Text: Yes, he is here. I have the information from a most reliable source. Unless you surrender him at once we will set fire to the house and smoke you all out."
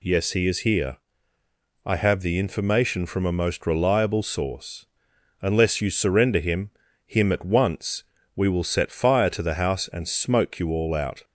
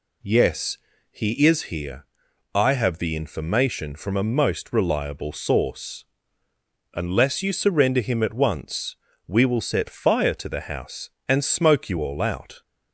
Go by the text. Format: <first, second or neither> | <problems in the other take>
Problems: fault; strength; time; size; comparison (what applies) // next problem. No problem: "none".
second | says "him" twice; at 7.0 s // pauses between "once" and "we"; slight; at 8.0 s; 0.32 s long; slight in the second